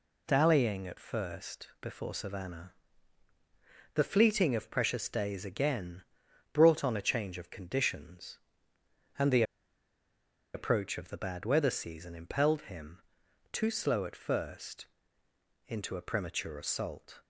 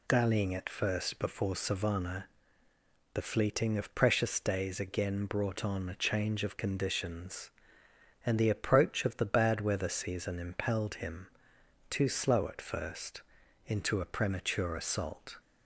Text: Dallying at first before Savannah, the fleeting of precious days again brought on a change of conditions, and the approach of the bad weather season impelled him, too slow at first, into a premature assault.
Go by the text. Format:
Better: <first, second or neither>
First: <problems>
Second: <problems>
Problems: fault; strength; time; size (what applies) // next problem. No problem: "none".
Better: second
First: pauses between "again" and "brought"; noticeable; at 6.0 s; 0.48 s long // pauses between "the" and "approach"; at 9.4 s; 1.1 s long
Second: none